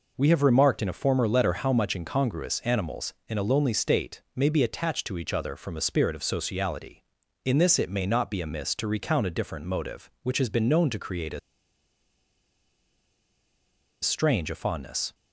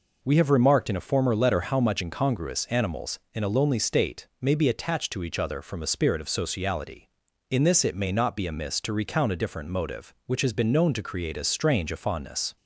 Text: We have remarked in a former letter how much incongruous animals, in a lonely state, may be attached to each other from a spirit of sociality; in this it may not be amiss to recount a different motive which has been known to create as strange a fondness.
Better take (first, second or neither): second